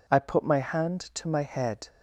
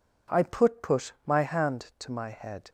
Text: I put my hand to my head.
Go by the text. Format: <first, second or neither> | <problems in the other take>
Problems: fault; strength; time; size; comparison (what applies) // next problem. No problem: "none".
first | says "put" twice; at 0.8 s